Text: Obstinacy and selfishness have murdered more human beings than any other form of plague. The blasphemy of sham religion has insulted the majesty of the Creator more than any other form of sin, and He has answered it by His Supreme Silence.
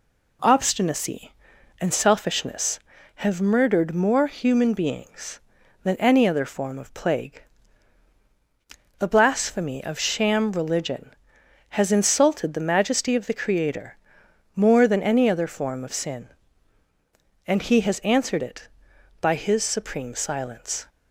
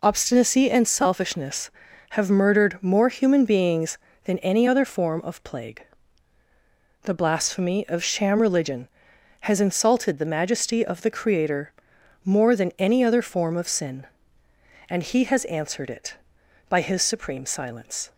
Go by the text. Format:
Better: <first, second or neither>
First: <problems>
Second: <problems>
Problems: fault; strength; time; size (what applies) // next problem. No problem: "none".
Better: neither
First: pauses between "Creator" and "more"; noticeable; at 13.9 s; 0.58 s long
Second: pauses between "Creator" and "more"; noticeable; at 11.7 s; 0.52 s long